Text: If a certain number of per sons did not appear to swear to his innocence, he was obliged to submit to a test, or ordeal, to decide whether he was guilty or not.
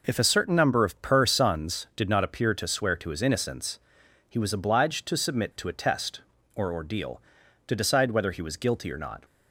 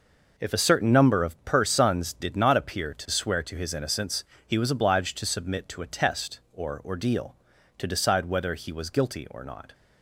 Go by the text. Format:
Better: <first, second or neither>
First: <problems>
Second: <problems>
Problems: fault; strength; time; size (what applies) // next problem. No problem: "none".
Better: neither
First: none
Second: none